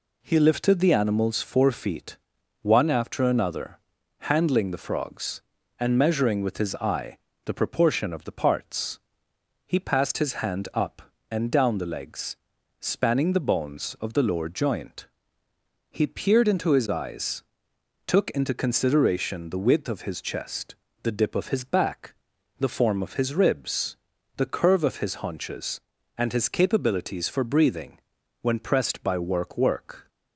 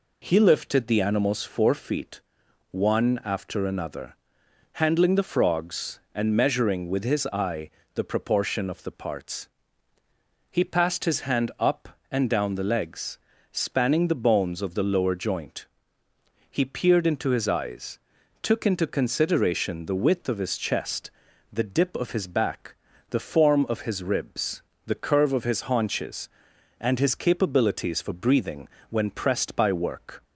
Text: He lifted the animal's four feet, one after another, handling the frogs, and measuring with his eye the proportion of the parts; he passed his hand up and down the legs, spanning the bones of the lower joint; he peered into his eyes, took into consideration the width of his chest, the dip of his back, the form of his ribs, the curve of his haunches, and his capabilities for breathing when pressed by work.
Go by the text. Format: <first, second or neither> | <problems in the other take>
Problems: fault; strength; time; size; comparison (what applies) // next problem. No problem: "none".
second | pauses between "eye" and "the"; slight; at 7.1 s; 0.28 s long; slight in the second // pauses between "breathing" and "when"; at 27.9 s; 0.42 s long; slight in the second // says "work" twice; at 29.5 s